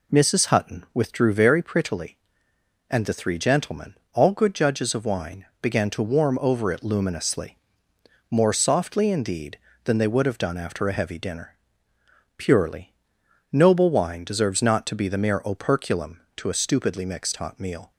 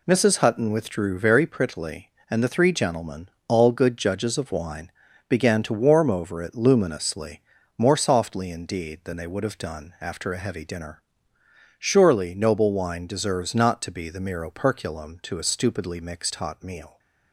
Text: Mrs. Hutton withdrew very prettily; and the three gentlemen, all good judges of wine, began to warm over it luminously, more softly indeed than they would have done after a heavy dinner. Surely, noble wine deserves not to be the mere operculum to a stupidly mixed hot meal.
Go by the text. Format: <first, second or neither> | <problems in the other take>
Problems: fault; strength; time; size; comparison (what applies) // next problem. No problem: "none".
second | says "Purely" for "Surely"; at 12.3 s